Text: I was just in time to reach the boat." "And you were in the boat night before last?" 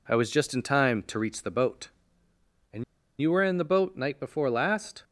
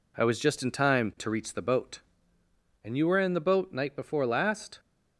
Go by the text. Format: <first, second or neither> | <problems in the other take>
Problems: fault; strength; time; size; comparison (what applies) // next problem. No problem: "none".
second | pauses between "And" and "you"; at 2.8 s; 0.37 s long